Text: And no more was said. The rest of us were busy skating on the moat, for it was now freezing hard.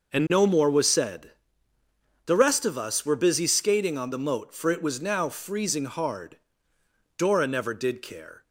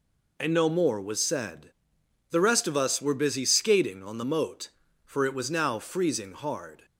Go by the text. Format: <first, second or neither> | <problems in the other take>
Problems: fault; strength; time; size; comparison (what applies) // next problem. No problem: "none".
second | goes on to say "Dora never did care"; noticeable; from 7.1 s on; 1.2 s long